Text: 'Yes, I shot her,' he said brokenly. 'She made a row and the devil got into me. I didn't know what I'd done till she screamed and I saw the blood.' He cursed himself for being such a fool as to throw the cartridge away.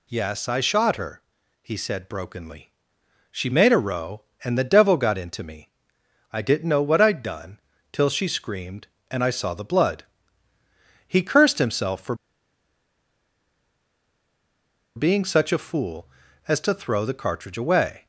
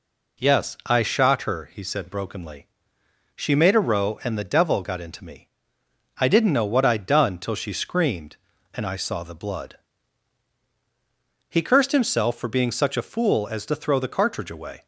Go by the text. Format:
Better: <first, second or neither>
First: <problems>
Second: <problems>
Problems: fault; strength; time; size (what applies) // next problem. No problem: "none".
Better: second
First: pauses between "done" and "till"; slight; at 7.6 s; 0.32 s long // pauses between "for" and "being"; strong; at 12.1 s; 2.8 s long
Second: none